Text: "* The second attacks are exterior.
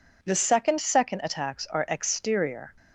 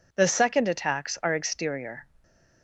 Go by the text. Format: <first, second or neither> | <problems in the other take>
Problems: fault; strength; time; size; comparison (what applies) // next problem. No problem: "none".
second | says "second" twice; at 0.7 s